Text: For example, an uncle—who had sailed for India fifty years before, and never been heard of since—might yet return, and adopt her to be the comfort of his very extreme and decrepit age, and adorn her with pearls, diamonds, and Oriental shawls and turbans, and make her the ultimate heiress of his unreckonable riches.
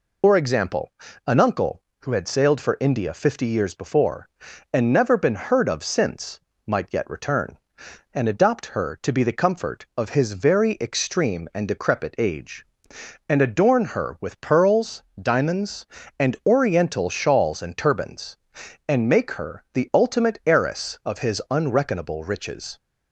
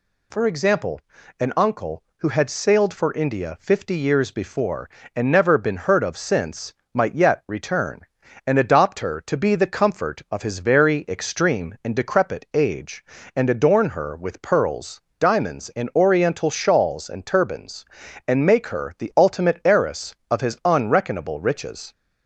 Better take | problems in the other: second | loses the start of "For"; at 0.2 s; 65 ms

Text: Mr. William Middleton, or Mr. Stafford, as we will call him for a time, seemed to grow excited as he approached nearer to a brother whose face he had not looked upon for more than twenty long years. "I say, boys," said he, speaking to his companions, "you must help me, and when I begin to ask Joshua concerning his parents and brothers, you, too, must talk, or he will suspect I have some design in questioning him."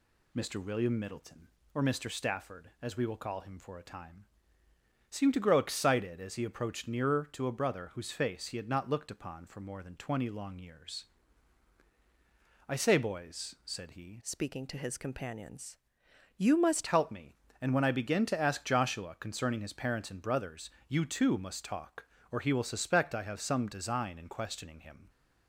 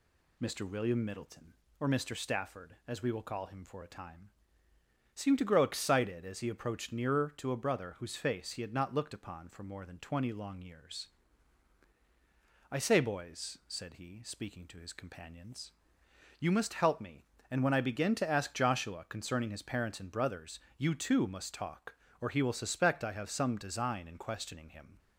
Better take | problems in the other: second | changes voice from "speaking" to "must"; from 14.2 to 16.8 s; 2.6 s long

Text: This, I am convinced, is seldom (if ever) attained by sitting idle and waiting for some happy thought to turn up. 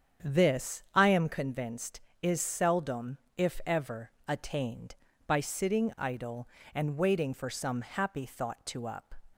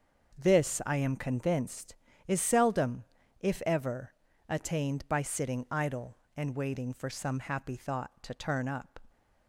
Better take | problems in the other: second | starts louder than the rest; strong; until 1.3 s; 8 dB; noticeable in the second // skips "turn"; at 8.8 s

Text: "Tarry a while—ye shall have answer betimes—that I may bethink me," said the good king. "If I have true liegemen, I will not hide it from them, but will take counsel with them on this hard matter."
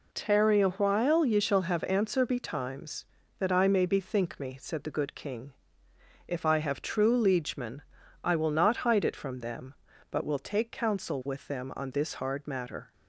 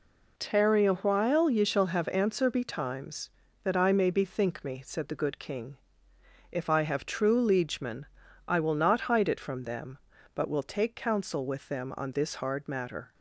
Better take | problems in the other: neither | none

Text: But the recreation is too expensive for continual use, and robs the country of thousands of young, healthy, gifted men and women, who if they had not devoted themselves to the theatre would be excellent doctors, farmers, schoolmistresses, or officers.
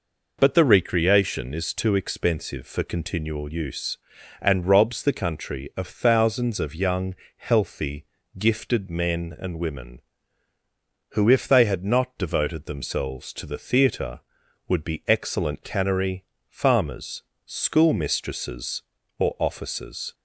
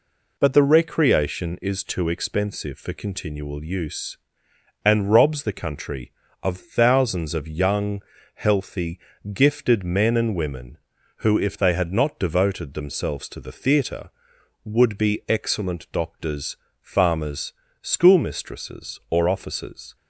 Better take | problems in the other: second | says "cannery" for "doctors"; at 15.6 s

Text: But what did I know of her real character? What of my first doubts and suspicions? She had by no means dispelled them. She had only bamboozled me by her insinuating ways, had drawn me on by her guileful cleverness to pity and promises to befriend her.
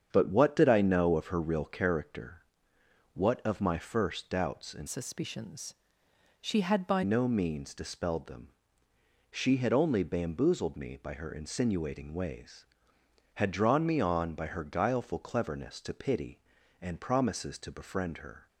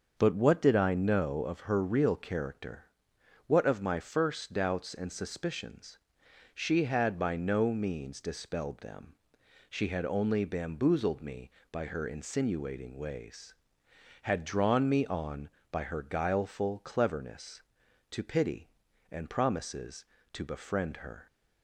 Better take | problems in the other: second | starts louder than the rest; strong; until 1.1 s; 8 dB; also in the second // changes voice from "suspicions" to "by"; from 4.8 to 7.0 s; 2.2 s long

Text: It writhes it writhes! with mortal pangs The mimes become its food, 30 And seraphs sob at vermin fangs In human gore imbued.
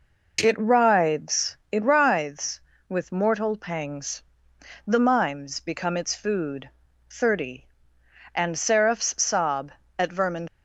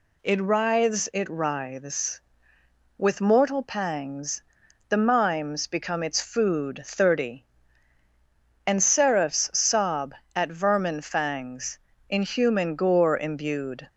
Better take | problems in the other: second | pauses between "pangs" and "The"; noticeable; at 4.2 s; 0.66 s long; noticeable in the second // stops before "fangs In human gore imbued"; at 10.4 s

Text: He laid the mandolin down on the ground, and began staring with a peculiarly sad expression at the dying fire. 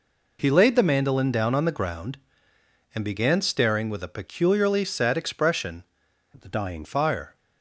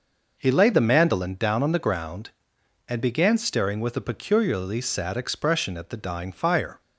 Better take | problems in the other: second | changes voice from "at" to "dying"; from 6.3 to 6.8 s; 0.5 s long

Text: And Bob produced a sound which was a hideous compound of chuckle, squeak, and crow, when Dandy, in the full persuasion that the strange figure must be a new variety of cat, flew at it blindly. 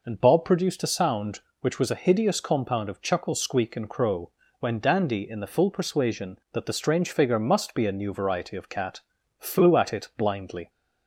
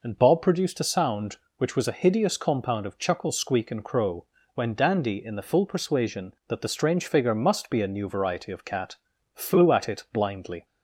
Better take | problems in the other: neither | none

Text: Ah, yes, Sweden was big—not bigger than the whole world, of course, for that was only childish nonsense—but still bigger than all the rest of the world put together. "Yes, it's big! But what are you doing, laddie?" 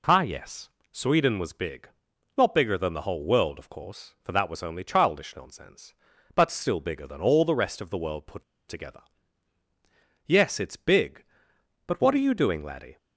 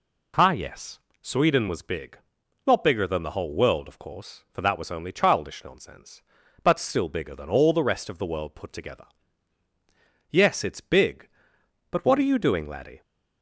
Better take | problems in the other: second | pauses between "put" and "together"; slight; at 8.4 s; 0.25 s long

